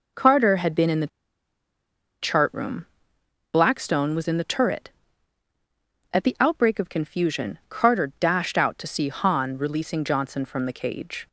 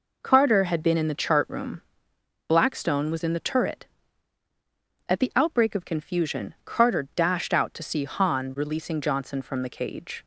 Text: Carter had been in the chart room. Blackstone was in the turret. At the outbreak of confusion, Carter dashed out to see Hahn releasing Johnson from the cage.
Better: second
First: pauses between "the" and "chart"; at 1.0 s; 1.1 s long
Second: none

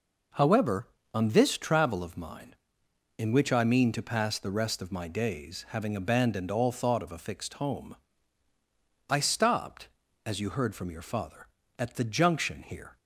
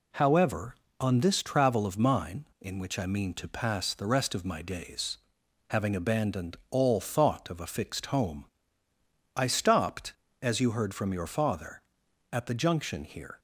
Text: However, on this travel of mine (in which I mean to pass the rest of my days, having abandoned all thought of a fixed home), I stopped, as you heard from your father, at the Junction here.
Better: neither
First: none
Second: none

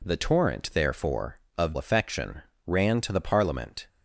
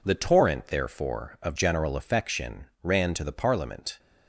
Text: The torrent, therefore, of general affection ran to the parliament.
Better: second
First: skips "general"; at 1.7 s // pauses between "affection" and "ran"; slight; at 2.4 s; 0.26 s long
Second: pauses between "affection" and "ran"; slight; at 2.6 s; 0.18 s long

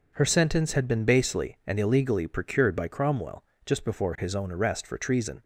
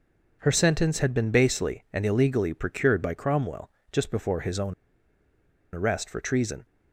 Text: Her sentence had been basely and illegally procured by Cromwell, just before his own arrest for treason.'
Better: first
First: none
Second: pauses between "own" and "arrest"; at 4.7 s; 1.0 s long

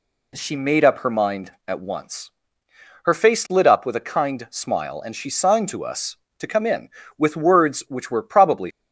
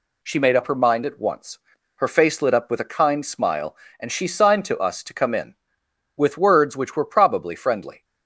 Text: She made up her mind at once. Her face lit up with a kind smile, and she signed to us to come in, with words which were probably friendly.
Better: second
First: stops before "friendly"; at 8.7 s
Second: none

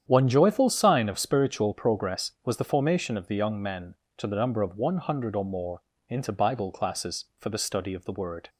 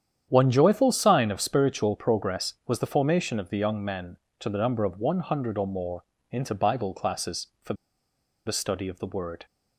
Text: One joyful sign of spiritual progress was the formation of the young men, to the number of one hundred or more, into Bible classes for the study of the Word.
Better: first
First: starts louder than the rest; strong; until 1.0 s; 9 dB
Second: starts louder than the rest; strong; until 1.3 s; 9 dB // pauses between "for" and "the"; noticeable; at 7.7 s; 0.72 s long

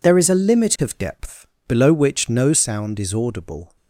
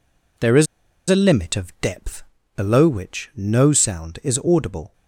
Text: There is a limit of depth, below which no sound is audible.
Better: first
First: none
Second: pauses between "is" and "a"; at 0.6 s; 0.44 s long

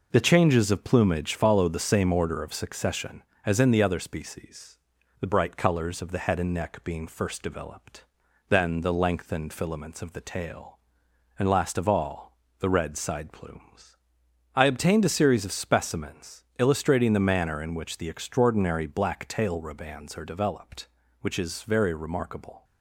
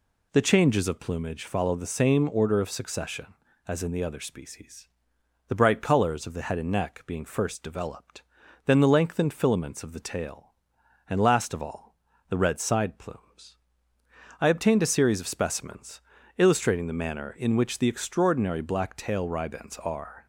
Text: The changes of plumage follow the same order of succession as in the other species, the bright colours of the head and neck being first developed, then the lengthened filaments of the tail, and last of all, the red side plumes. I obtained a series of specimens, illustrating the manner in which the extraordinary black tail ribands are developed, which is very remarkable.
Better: first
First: none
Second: stops before "developed which is very remarkable"; at 20.2 s

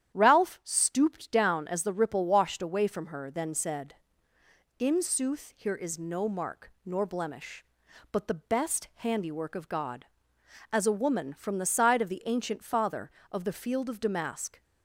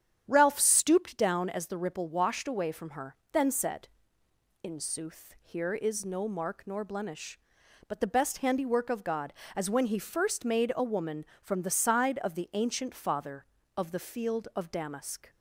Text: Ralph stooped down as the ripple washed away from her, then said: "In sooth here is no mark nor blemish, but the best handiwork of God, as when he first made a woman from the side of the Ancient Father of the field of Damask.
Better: second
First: starts louder than the rest; strong; until 1.2 s; 10.5 dB // skips "when he first made"; at 10.8 s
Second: starts louder than the rest; strong; until 1.2 s; 9 dB

